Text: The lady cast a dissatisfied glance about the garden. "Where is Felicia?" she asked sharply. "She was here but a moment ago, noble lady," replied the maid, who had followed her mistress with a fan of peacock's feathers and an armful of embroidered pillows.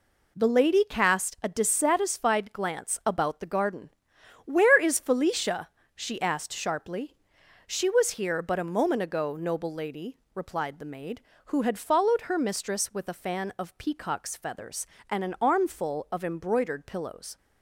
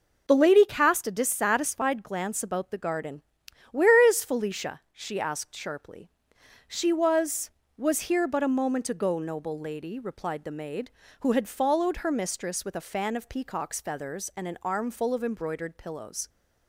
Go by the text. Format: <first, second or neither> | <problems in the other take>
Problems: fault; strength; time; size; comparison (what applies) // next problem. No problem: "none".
first | says "was" twice; at 7.7 s